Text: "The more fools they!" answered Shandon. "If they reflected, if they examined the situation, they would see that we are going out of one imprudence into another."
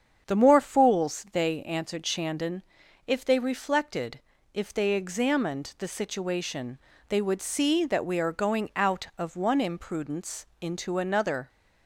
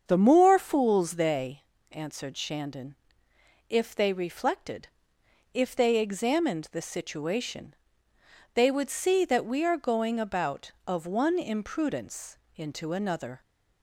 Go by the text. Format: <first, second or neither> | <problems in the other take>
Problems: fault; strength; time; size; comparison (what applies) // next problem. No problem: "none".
first | starts louder than the rest; until 1.1 s; 7 dB; strong in the first // says "about" for "out"; at 10.2 s // pauses between "imprudence" and "into"; slight; at 12.3 s; 0.18 s long; slight in the first